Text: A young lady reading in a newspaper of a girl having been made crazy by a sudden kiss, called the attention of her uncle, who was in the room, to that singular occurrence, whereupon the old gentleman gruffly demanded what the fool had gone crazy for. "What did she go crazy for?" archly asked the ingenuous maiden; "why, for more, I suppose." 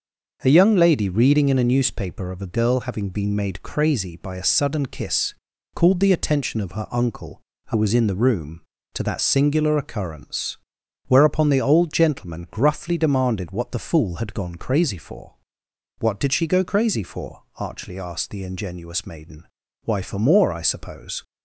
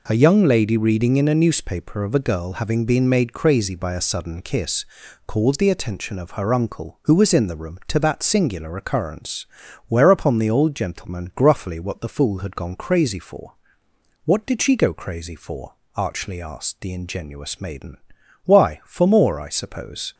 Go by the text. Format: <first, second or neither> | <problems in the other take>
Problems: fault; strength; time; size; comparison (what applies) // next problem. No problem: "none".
first | skips "demanded"; at 11.8 s